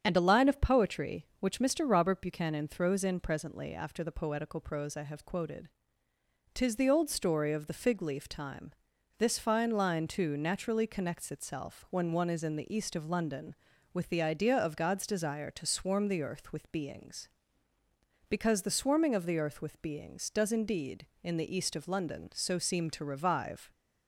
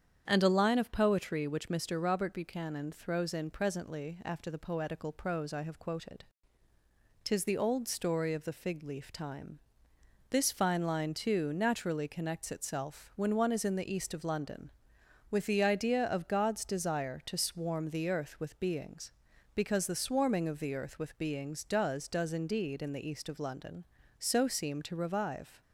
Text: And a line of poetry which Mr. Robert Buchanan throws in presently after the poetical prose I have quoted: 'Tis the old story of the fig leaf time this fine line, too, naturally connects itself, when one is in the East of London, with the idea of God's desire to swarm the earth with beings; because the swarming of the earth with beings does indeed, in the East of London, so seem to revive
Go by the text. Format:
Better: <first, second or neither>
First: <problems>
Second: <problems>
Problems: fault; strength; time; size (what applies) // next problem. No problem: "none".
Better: first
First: starts louder than the rest; strong; until 1.0 s; 8 dB // pauses between "time" and "this"; noticeable; at 8.7 s; 0.46 s long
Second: starts louder than the rest; strong; until 1.2 s; 8.5 dB // pauses between "time" and "this"; noticeable; at 9.5 s; 0.72 s long // says "does" twice; at 22.0 s